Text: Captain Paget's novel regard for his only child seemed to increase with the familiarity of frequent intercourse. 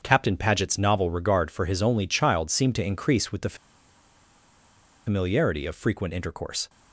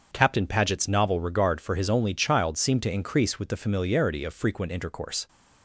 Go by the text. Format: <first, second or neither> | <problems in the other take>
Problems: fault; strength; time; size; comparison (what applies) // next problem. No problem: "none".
second | starts louder than the rest; until 1.0 s; 6.5 dB; also in the second // pauses between "the" and "familiarity"; strong; at 3.5 s; 1.5 s long